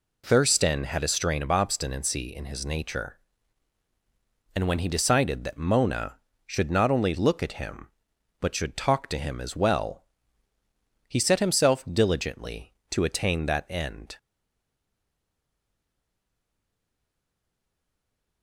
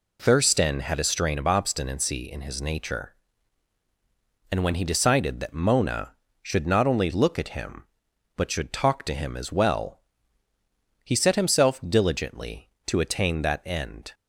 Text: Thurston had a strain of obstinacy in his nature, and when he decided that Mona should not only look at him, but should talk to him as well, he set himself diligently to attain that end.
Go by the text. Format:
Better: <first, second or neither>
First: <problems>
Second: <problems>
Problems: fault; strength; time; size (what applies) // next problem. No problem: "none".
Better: second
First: stays silent after the last word; strong; from 14.1 s on; 4.3 s long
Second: none